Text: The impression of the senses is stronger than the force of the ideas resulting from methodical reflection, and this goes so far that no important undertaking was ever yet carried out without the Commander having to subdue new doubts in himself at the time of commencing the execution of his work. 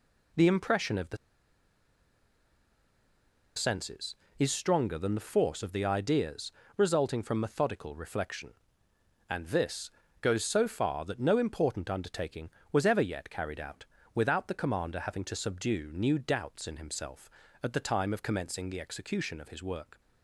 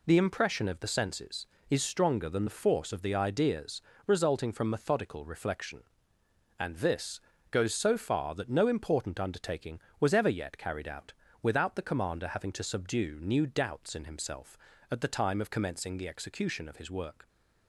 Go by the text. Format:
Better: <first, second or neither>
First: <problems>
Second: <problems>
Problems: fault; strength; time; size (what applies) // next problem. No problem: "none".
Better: second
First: pauses between "the" and "senses"; strong; at 1.1 s; 2.3 s long // pauses between "ideas" and "resulting"; slight; at 6.5 s; 0.26 s long // pauses between "this" and "goes"; slight; at 9.8 s; 0.32 s long // pauses between "out" and "without"; slight; at 13.8 s; 0.30 s long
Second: pauses between "ideas" and "resulting"; slight; at 3.8 s; 0.26 s long // pauses between "this" and "goes"; slight; at 7.1 s; 0.32 s long // pauses between "out" and "without"; slight; at 11.1 s; 0.30 s long